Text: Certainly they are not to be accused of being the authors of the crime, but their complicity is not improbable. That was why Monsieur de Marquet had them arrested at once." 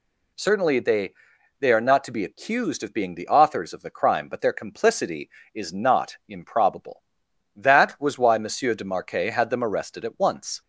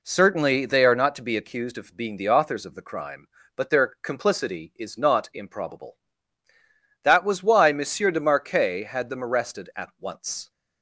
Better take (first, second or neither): second